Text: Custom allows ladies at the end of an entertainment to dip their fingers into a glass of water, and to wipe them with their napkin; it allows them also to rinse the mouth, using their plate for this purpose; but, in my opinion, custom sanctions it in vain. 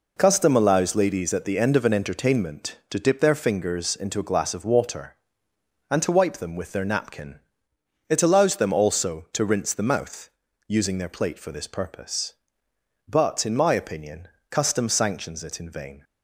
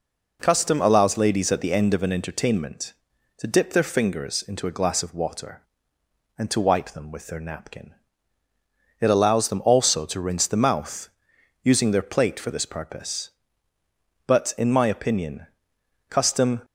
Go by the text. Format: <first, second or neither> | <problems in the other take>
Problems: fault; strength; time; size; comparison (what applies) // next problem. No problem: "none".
first | stops before "sanctions it in vain"; at 16.6 s